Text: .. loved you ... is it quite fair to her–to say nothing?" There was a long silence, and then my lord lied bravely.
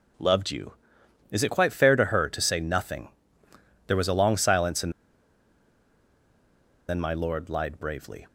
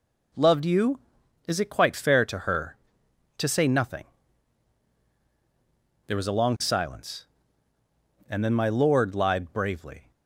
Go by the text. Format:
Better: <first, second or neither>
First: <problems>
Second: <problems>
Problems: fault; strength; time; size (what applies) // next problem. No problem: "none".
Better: second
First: pauses between "and" and "then"; strong; at 4.9 s; 1.9 s long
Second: none